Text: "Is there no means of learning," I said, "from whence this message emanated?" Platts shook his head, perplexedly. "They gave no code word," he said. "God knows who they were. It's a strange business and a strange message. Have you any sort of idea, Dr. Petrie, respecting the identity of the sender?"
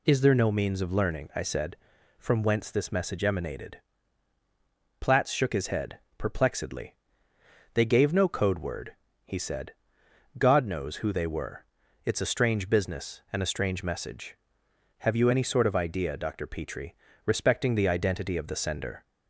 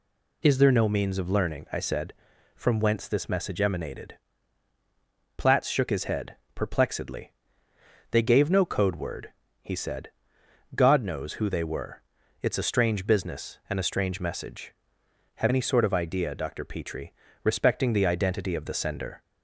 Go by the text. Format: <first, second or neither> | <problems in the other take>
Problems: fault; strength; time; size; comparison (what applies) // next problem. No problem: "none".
first | skips "you"; at 15.4 s